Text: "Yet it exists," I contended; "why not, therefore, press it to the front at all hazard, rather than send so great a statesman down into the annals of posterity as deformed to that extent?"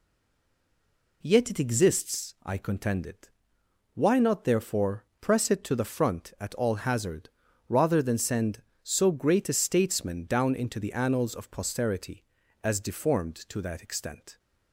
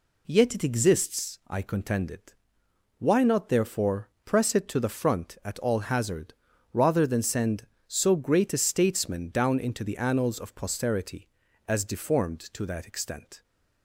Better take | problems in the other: second | stays silent before the first word; noticeable; until 1.2 s; 1.2 s long

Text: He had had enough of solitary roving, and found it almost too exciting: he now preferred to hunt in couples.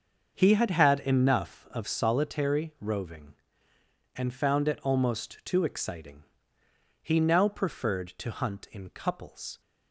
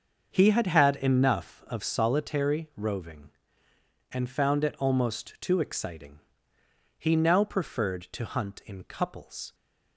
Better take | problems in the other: neither | starts louder than the rest; the same in both

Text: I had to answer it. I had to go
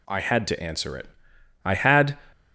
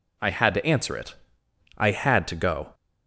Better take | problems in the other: second | stops before "to go"; at 2.3 s

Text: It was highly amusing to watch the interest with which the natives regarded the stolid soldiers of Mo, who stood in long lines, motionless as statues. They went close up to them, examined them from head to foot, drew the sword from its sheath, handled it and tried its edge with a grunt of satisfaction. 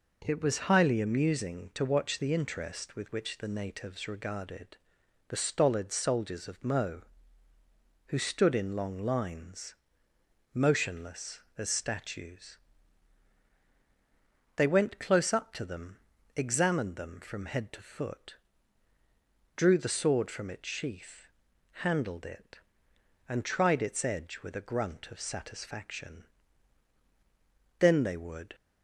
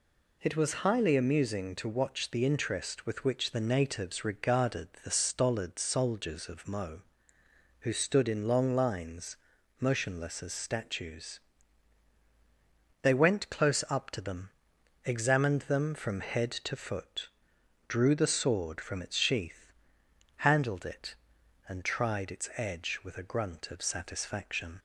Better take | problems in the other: second | pauses between "regarded" and "the"; noticeable; at 4.7 s; 0.50 s long; slight in the second // goes on to say "Then they would"; noticeable; from 27.7 s on; 0.76 s long

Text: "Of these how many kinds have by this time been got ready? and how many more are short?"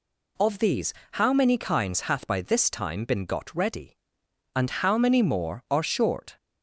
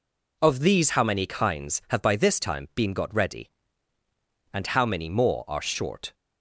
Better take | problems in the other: second | pauses between "these" and "how"; slight; at 0.9 s; 0.20 s long // says "hath" for "have"; at 2.0 s

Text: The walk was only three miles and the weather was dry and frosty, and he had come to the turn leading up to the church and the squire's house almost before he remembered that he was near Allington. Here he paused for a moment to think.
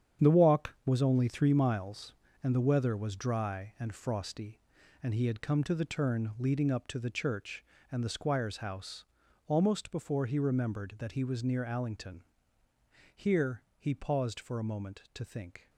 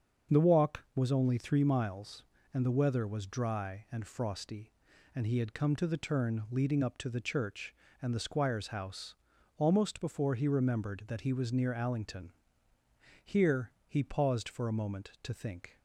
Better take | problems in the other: second | gets quieter; strong; throughout; 10 dB // starts louder than the rest; strong; until 1.3 s; 8.5 dB; also in the second // pauses between "house" and "almost"; at 9.0 s; 0.40 s long; also in the second // pauses between "Here" and "he"; slight; at 13.6 s; 0.16 s long; slight in the second

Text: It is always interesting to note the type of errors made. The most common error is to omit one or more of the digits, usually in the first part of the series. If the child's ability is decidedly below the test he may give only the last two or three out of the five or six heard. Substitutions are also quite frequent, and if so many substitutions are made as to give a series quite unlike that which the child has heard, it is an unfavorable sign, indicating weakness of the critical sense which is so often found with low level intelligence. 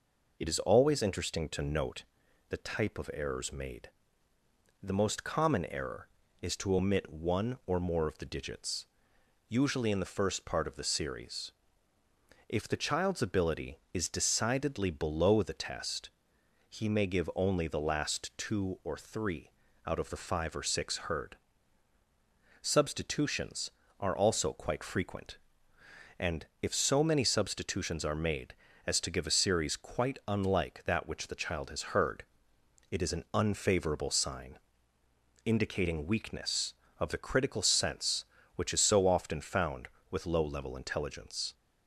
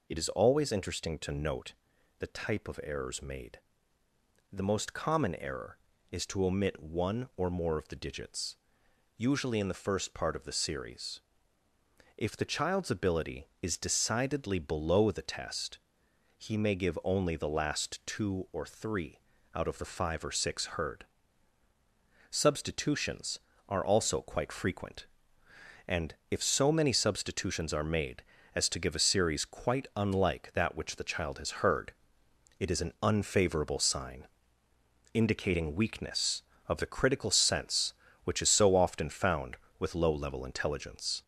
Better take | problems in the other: first | gets louder; noticeable; throughout; 4 dB // pauses between "note" and "the"; at 1.7 s; 0.44 s long; also in the first // pauses between "test" and "he"; noticeable; at 15.7 s; 0.60 s long; noticeable in the first // pauses between "three" and "out"; slight; at 19.2 s; 0.34 s long; slight in the first // pauses between "and" and "if"; slight; at 26.1 s; 0.16 s long; slight in the first

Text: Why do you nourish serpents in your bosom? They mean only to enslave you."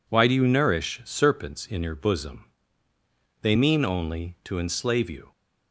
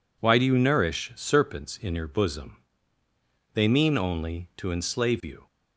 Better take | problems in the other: neither | none

